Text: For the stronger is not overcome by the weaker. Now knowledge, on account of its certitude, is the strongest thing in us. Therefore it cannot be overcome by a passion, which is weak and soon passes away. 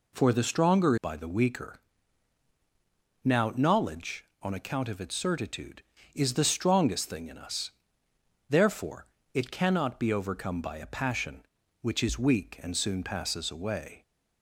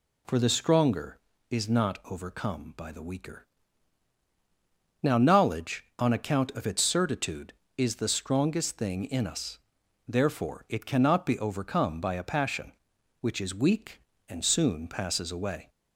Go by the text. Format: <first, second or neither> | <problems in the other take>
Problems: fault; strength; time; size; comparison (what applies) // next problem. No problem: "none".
second | skips "is not overcome"; at 0.9 s // pauses between "Therefore" and "it"; slight; at 9.0 s; 0.28 s long